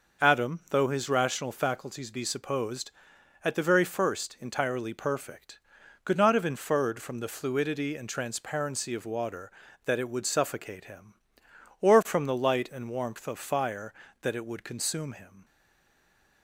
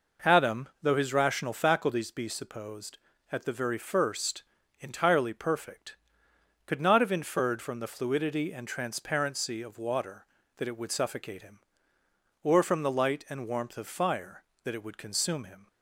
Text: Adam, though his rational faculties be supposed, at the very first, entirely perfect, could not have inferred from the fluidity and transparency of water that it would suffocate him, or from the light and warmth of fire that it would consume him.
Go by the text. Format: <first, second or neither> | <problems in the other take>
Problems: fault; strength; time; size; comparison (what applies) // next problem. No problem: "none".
second | stays silent after the last word; from 15.4 s on; 1.0 s long